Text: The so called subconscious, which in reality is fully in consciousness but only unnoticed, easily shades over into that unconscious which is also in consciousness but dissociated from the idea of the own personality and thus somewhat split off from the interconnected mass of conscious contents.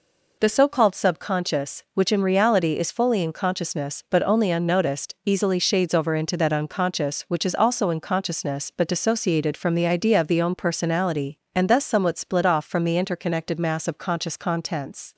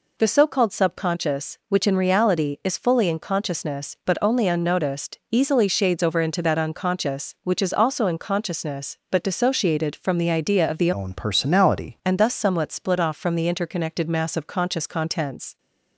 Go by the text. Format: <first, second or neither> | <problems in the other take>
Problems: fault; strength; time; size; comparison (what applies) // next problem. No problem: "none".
first | changes voice from "own" to "personality"; from 10.9 to 11.9 s; 1.0 s long